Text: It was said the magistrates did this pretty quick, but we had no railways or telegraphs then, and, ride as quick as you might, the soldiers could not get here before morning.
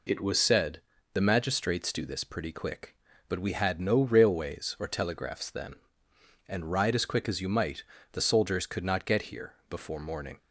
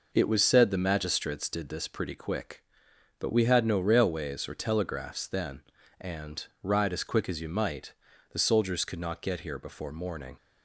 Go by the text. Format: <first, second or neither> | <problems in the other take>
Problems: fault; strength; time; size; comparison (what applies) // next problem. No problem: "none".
second | pauses between "said" and "the"; slight; at 0.7 s; 0.32 s long // says "do" for "did"; at 1.9 s